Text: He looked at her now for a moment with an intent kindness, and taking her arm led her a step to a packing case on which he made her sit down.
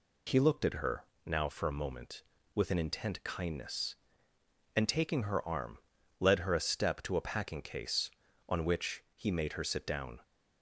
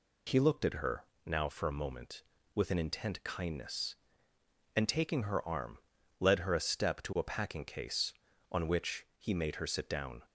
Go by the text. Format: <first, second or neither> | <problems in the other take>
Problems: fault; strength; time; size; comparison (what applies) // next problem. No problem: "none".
neither | pauses between "her" and "now"; slight; the same in both // pauses between "arm" and "led"; the same in both